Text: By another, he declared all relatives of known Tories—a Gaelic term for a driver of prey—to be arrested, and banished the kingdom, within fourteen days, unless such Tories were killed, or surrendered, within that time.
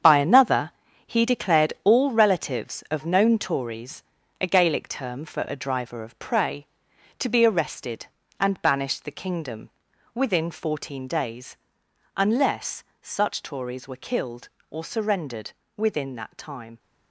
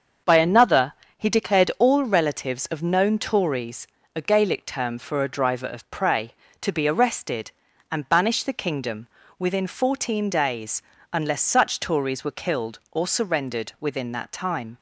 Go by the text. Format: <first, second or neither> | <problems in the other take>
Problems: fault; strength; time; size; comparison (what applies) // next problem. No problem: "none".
second | gets quieter; strong; throughout; 8.5 dB // starts louder than the rest; strong; until 1.3 s; 7.5 dB; also in the second // pauses between "unless" and "such"; slight; at 12.8 s; 0.20 s long